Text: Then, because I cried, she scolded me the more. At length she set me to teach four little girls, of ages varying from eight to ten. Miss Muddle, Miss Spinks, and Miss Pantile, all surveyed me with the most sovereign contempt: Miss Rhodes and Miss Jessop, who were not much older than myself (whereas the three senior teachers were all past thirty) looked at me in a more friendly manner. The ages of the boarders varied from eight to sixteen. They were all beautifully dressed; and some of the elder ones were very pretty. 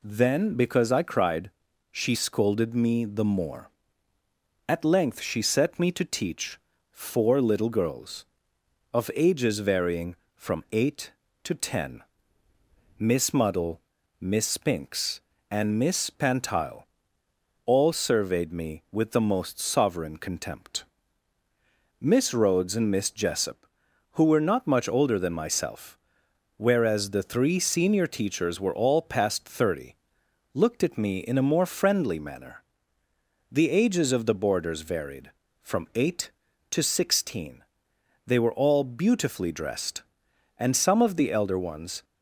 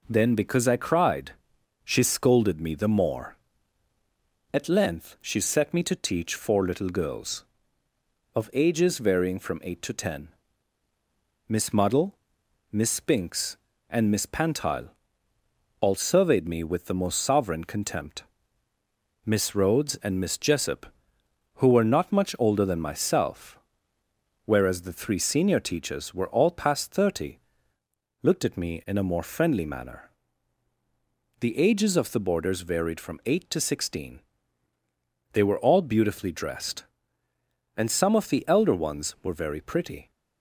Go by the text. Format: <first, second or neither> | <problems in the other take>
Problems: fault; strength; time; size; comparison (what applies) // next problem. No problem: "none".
second | pauses between "teach" and "four"; slight; at 6.5 s; 0.32 s long // stops before "were very pretty"; at 42.0 s